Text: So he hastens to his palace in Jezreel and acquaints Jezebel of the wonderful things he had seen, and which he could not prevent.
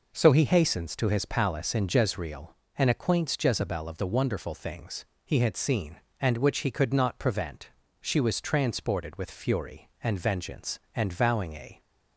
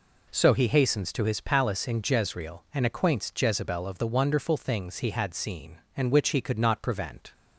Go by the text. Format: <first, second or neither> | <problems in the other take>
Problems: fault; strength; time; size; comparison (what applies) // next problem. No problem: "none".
second | pauses between "things" and "he"; slight; at 5.0 s; 0.20 s long // goes on to say "She was transported with fury and vengeance and vowing a"; strong; from 8.0 s on; 3.8 s long